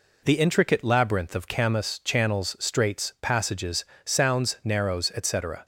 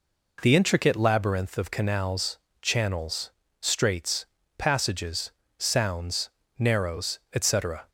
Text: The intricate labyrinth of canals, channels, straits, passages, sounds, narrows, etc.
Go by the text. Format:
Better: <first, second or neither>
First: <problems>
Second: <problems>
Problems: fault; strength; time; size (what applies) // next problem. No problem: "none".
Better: second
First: says "camas" for "canals"; at 1.4 s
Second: none